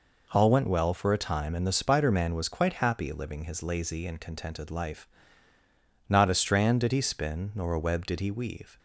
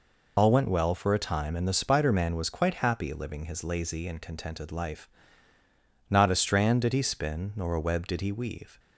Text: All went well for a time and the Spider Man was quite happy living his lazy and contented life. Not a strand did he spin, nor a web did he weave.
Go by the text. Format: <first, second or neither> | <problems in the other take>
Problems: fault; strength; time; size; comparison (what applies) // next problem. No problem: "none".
first | loses the start of "All"; at 0.3 s; 60 ms